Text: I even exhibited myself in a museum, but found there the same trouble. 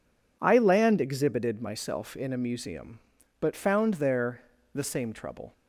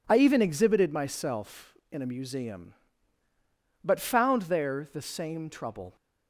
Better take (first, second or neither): second